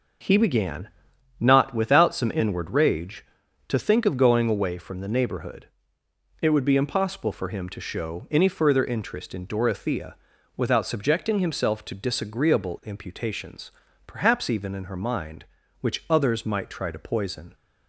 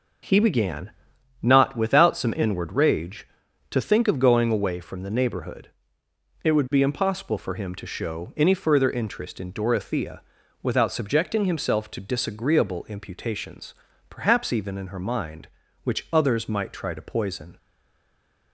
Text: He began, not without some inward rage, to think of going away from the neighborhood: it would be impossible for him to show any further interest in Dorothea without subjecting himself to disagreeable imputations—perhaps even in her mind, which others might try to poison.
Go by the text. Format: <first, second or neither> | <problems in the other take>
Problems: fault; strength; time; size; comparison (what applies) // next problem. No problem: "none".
first | pauses between "Dorothea" and "without"; at 10.2 s; 0.40 s long; also in the first // stays silent after the last word; slight; from 17.5 s on; 1.0 s long